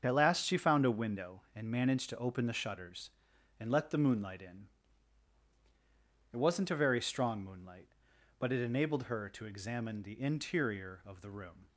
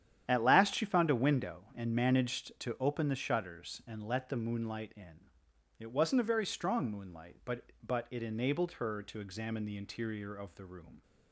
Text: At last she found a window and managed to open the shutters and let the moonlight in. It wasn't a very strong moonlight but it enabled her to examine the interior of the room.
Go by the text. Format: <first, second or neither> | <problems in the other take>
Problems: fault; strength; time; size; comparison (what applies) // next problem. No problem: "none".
first | starts louder than the rest; strong; until 1.2 s; 10 dB; also in the first // says "but" twice; at 7.8 s